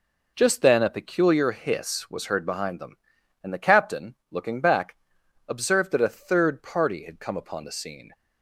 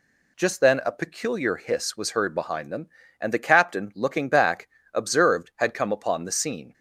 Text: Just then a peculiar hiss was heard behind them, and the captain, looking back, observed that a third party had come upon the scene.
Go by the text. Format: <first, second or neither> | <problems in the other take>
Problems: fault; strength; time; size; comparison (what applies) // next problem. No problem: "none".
first | skips "that a third party"; at 5.5 s